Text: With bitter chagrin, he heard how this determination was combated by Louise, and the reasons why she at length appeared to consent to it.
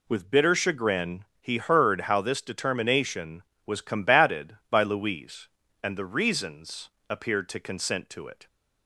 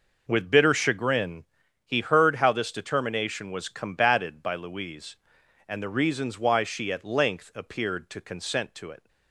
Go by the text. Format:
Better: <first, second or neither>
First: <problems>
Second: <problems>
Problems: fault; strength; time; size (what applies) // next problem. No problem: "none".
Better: second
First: skips "why she at length"; at 7.0 s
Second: none